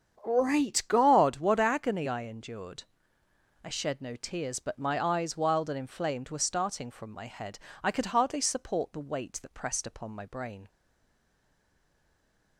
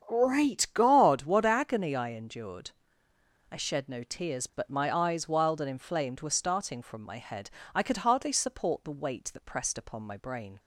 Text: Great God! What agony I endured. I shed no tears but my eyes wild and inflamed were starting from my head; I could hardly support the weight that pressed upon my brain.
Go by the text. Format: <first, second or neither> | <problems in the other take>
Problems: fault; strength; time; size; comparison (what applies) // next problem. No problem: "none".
second | starts louder than the rest; strong; until 1.2 s; 8 dB; strong in the second // stays silent after the last word; noticeable; from 10.6 s on; 1.9 s long